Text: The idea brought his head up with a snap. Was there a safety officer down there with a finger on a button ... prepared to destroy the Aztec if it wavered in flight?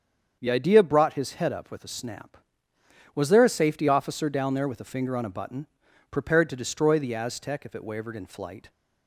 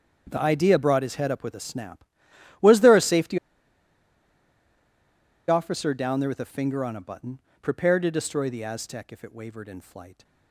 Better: first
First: starts louder than the rest; strong; until 1.4 s; 7 dB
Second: starts louder than the rest; strong; until 1.3 s; 7.5 dB // pauses between "safety" and "officer"; strong; at 3.3 s; 2.1 s long

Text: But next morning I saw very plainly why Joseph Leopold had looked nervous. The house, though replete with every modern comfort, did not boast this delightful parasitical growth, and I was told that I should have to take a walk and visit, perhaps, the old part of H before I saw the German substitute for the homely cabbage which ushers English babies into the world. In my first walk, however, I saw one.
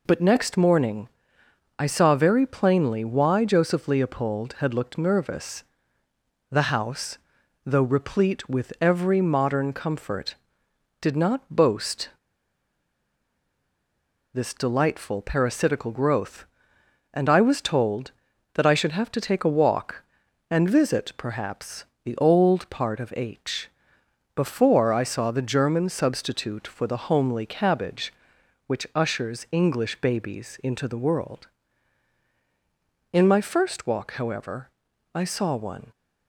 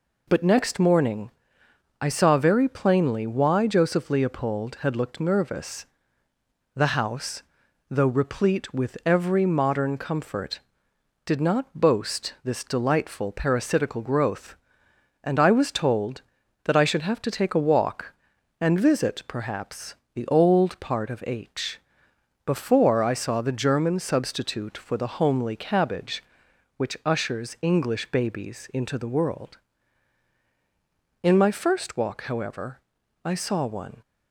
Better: second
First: pauses between "morning" and "I"; noticeable; at 1.0 s; 0.70 s long // pauses between "boast" and "this"; strong; at 12.0 s; 2.2 s long // pauses between "H" and "before"; noticeable; at 23.6 s; 0.66 s long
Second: pauses between "morning" and "I"; noticeable; at 1.3 s; 0.70 s long // pauses between "H" and "before"; noticeable; at 21.7 s; 0.66 s long

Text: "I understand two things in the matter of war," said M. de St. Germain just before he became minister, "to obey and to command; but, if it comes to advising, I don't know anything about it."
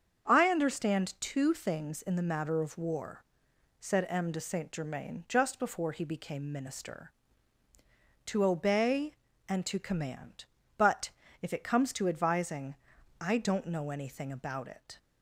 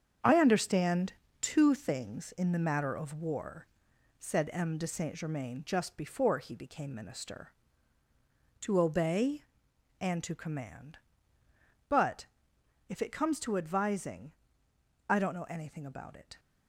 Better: first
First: starts louder than the rest; strong; until 1.3 s; 7.5 dB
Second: gets quieter; strong; throughout; 8 dB // starts louder than the rest; strong; until 1.5 s; 7.5 dB // pauses between "understand" and "two"; slight; at 1.1 s; 0.28 s long

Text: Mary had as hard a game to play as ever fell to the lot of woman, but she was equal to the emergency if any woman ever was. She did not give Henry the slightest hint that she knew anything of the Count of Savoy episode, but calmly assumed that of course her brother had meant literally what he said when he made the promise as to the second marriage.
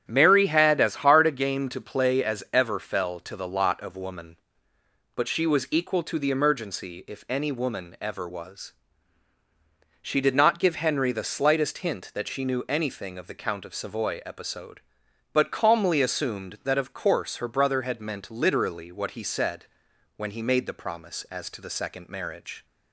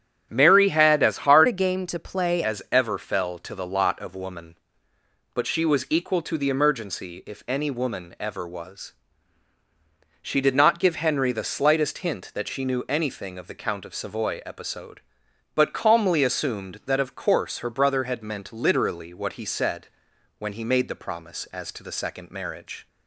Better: first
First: starts louder than the rest; strong; until 1.0 s; 9.5 dB // pauses between "said" and "when"; noticeable; at 19.6 s; 0.50 s long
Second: starts louder than the rest; strong; until 1.3 s; 8 dB // changes voice from "a" to "play"; from 1.4 to 2.4 s; 1.0 s long // pauses between "said" and "when"; noticeable; at 19.8 s; 0.50 s long

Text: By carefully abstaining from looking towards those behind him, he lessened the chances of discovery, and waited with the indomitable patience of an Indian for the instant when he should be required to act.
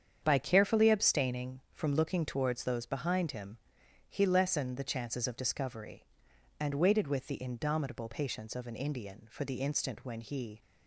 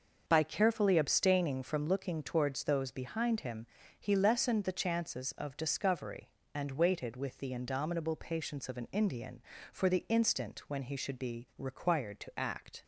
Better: second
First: starts louder than the rest; strong; until 1.2 s; 8 dB // stops before "should be required to act"; at 10.6 s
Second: starts louder than the rest; until 1.2 s; 6 dB

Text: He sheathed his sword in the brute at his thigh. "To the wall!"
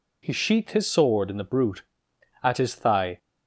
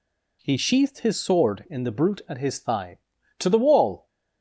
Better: second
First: stops before "To the wall"; at 3.1 s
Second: none

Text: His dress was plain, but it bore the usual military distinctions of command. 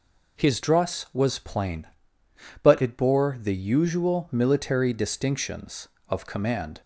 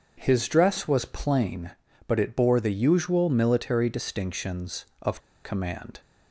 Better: first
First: none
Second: starts louder than the rest; until 1.2 s; 7 dB // pauses between "of" and "command"; slight; at 5.2 s; 0.23 s long

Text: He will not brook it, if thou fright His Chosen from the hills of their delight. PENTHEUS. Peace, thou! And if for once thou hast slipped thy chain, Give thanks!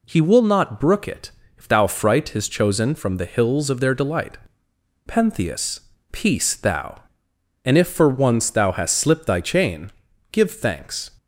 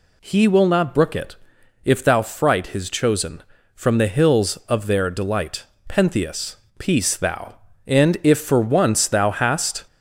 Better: first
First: none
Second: stops before "slipped thy chain Give thanks"; at 9.8 s

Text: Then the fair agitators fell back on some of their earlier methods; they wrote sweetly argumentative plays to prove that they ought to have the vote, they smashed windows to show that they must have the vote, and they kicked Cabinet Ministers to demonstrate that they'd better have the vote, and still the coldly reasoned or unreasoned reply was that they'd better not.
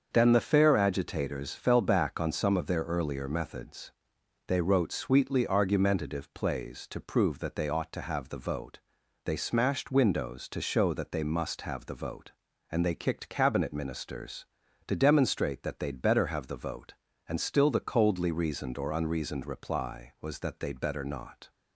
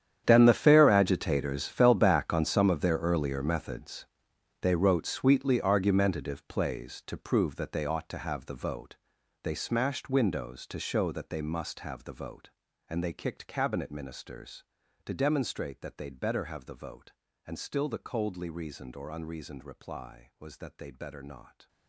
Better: first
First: starts louder than the rest; until 1.1 s; 6.5 dB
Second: gets quieter; strong; throughout; 18 dB // starts louder than the rest; strong; until 1.2 s; 9.5 dB

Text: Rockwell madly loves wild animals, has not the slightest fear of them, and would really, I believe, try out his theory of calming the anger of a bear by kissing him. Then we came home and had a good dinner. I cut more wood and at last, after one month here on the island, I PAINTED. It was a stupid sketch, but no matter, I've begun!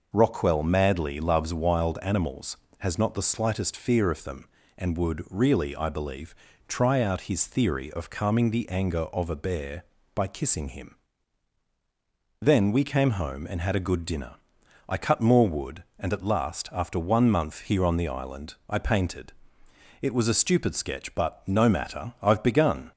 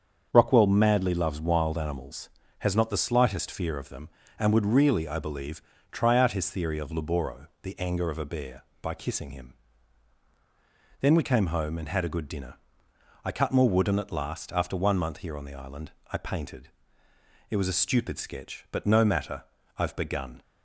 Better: first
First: none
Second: starts louder than the rest; strong; until 1.3 s; 7 dB // says "laboro" for "calming"; at 6.9 s

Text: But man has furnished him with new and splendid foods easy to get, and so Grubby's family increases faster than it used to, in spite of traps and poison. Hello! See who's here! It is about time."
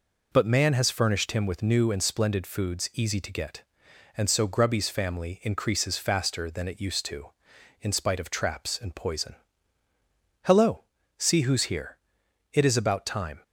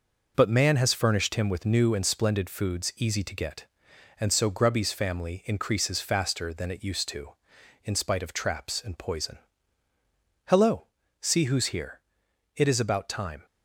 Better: first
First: none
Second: gets quieter; noticeable; throughout; 5 dB

